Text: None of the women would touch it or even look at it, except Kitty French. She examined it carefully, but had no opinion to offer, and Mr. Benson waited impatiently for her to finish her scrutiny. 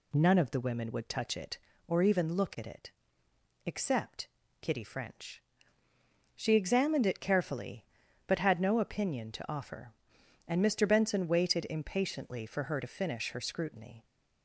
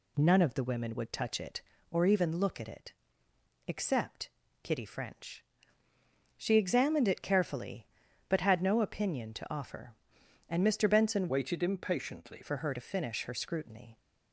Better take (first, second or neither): first